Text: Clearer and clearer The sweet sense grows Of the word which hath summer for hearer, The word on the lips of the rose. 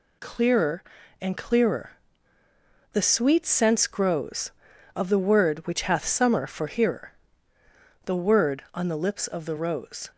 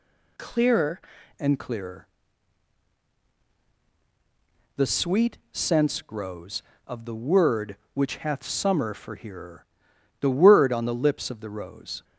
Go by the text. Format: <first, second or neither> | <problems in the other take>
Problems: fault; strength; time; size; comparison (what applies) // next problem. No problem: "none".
first | changes voice at "and"; from 1.3 s on; 10.7 s long // pauses between "clearer" and "The"; strong; at 2.0 s; 2.7 s long; also in the first